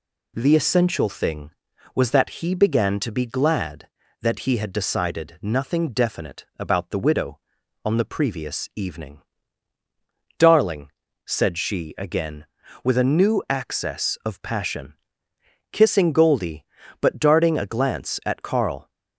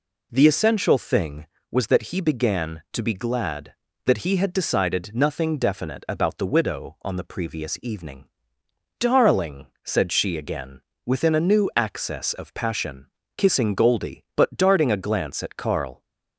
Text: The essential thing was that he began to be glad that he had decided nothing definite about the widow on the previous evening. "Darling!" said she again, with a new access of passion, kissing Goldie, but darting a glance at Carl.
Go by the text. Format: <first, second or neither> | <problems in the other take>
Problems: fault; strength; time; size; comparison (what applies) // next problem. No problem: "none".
first | says "within" for "with"; at 11.0 s